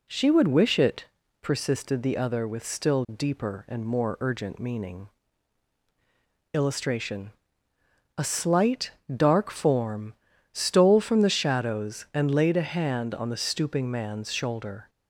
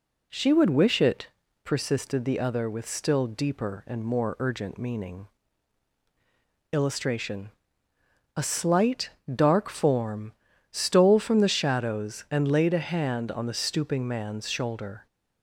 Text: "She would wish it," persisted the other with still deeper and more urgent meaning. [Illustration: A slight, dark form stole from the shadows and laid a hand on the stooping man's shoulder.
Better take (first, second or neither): neither